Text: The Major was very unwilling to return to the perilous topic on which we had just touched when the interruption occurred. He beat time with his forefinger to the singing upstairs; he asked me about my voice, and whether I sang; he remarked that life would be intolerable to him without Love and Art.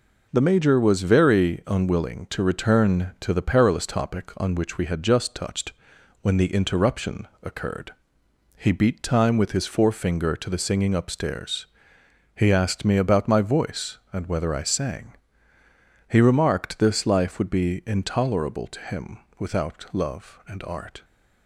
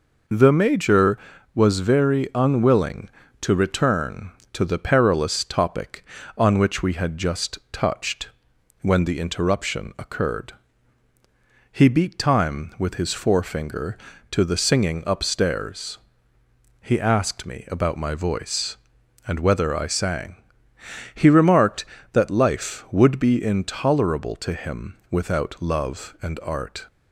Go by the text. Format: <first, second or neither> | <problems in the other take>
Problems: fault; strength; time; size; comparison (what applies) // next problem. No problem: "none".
second | pauses between "touched" and "when"; noticeable; at 5.7 s; 0.48 s long; noticeable in the second // pauses between "interruption" and "occurred"; slight; at 7.2 s; 0.16 s long // says "this" for "that"; at 16.7 s // pauses between "him" and "without"; slight; at 19.2 s; 0.18 s long